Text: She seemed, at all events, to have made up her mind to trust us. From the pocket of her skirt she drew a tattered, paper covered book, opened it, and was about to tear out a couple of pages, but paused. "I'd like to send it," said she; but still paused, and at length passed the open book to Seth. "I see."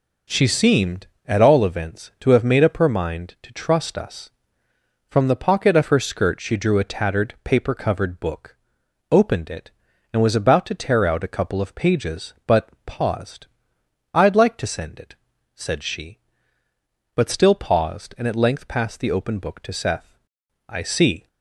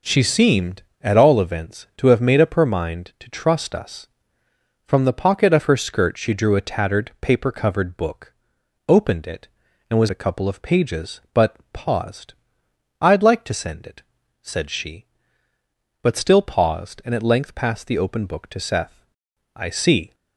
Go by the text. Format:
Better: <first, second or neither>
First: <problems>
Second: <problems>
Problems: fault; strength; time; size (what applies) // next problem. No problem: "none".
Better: first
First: pauses between "but" and "paused"; slight; at 12.6 s; 0.18 s long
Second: skips "about to tear out"; at 10.0 s // pauses between "but" and "paused"; slight; at 11.5 s; 0.18 s long